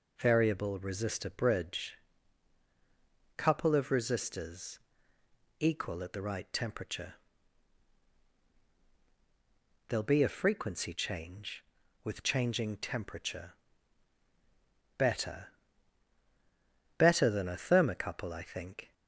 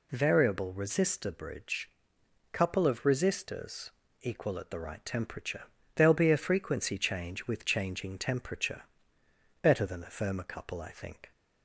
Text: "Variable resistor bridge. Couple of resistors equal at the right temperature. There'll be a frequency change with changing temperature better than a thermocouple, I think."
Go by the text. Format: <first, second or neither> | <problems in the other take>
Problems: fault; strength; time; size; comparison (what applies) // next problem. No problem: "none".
second | pauses between "resistors" and "equal"; noticeable; at 4.7 s; 0.82 s long; slight in the second // pauses between "temperature" and "better"; strong; at 13.5 s; 1.4 s long; noticeable in the second // says "better" twice; at 16.9 s